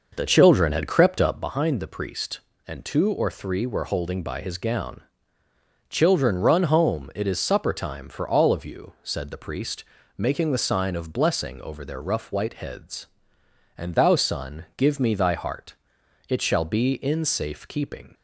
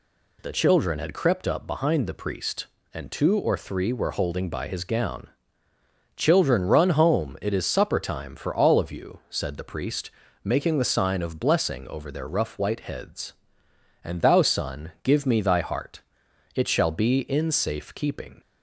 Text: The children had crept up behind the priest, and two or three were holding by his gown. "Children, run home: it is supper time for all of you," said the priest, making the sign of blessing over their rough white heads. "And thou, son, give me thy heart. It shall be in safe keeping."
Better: second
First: starts louder than the rest; noticeable; until 1.5 s; 5.5 dB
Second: none

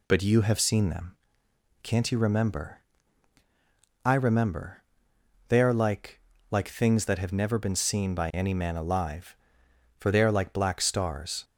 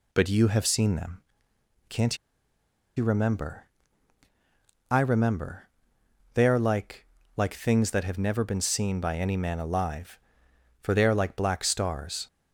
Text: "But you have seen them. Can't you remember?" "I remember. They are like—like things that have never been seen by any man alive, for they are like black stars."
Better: first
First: none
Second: pauses between "Can't" and "you"; noticeable; at 2.1 s; 0.79 s long

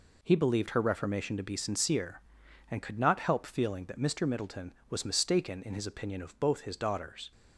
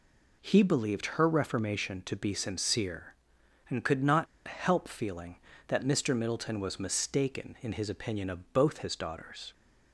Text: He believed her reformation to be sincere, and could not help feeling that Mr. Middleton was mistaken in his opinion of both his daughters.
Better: first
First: none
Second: pauses between "not" and "help"; slight; at 4.2 s; 0.22 s long

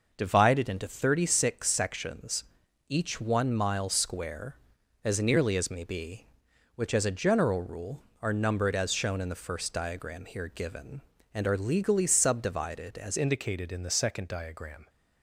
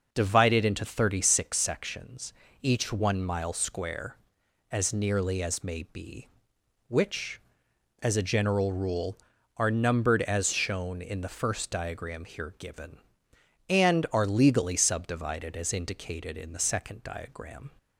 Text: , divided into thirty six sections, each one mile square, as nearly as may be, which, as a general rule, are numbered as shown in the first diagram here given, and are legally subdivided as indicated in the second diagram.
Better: second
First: changes voice at "indicated"; from 13.1 s on; 1.7 s long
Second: none

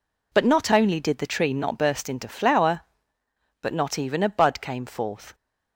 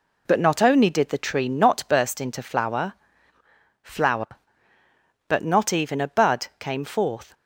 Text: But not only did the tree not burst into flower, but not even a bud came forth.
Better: first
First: none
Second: says "flower" twice; at 3.8 s

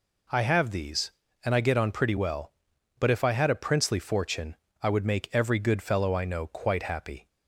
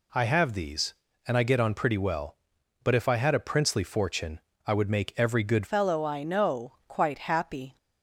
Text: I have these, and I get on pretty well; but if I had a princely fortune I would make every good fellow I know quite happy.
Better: first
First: pauses between "fortune" and "I"; slight; at 4.5 s; 0.26 s long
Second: pauses between "fortune" and "I"; slight; at 4.3 s; 0.26 s long // changes voice at "fellow"; from 5.6 s on; 2.1 s long

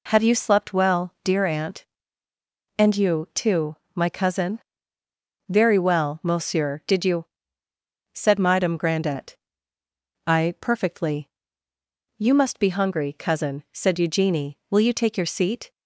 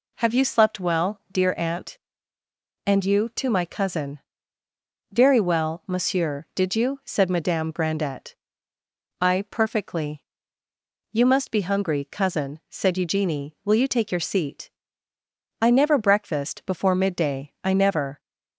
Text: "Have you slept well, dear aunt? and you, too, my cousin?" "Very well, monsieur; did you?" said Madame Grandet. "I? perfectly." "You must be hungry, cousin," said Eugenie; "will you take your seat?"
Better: first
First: none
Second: goes on to say "I never breakfast before midday I never"; strong; from 15.6 s on; 2.5 s long

